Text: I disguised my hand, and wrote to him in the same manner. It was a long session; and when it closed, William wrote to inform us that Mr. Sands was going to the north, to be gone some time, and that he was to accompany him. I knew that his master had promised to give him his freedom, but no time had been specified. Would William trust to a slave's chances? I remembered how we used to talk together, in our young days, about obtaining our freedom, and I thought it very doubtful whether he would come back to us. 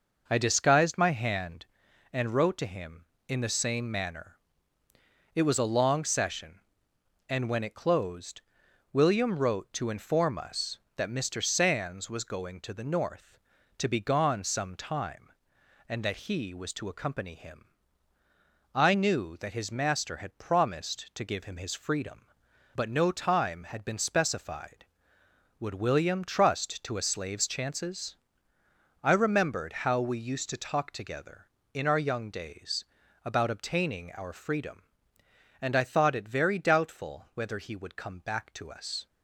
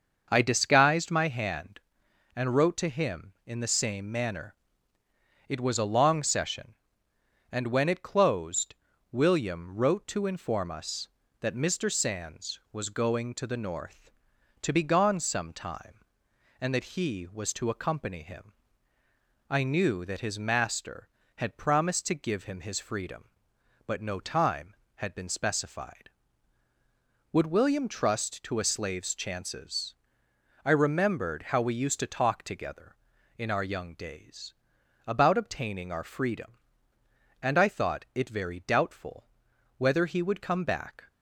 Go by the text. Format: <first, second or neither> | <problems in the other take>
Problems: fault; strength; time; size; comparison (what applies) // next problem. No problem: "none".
first | starts louder than the rest; until 1.3 s; 6.5 dB // pauses between "doubtful" and "whether"; noticeable; at 39.2 s; 0.50 s long // stops before "to us"; at 41.0 s